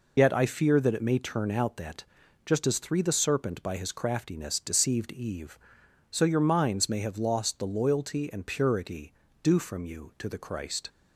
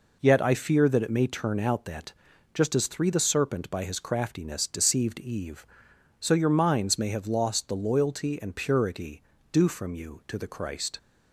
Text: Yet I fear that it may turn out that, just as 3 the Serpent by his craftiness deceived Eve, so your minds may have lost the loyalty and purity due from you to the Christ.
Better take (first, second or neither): second